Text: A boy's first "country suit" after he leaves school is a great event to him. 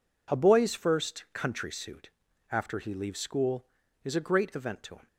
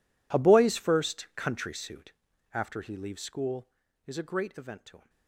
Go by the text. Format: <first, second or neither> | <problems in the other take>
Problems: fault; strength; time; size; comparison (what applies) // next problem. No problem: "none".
first | gets quieter; strong; throughout; 21.5 dB // pauses between "suit" and "after"; at 2.1 s; 0.40 s long; also in the first